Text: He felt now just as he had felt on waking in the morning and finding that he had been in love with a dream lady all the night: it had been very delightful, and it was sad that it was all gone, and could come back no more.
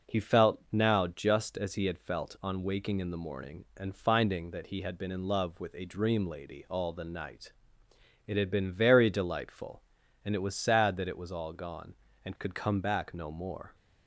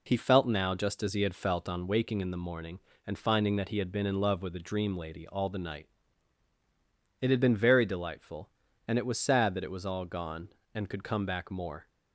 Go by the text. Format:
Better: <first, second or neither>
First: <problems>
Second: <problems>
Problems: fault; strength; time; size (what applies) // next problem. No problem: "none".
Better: first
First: none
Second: skips "no"; at 11.5 s